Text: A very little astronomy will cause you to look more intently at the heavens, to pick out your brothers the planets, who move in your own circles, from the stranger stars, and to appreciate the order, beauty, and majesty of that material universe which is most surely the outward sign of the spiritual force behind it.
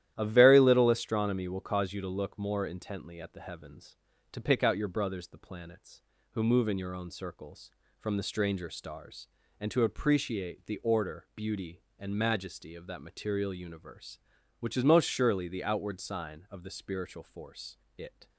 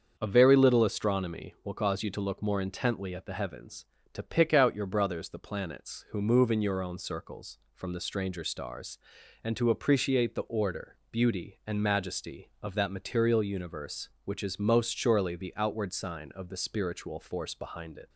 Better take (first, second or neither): second